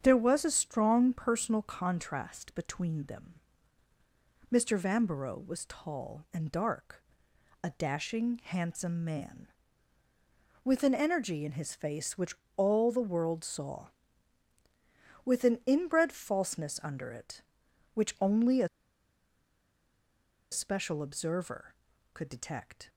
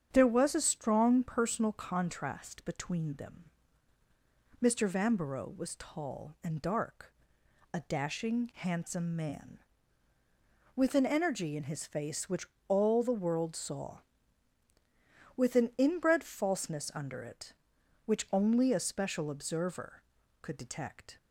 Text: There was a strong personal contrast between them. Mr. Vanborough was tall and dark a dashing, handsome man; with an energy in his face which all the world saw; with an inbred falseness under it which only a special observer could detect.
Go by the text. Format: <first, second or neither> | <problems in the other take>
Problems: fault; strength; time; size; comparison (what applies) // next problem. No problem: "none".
second | starts louder than the rest; strong; until 1.0 s; 8 dB; strong in the second // pauses between "dark" and "a"; noticeable; at 7.0 s; 0.62 s long; noticeable in the second // pauses between "which" and "all"; slight; at 12.3 s; 0.22 s long; slight in the second // pauses between "a" and "special"; strong; at 18.6 s; 1.8 s long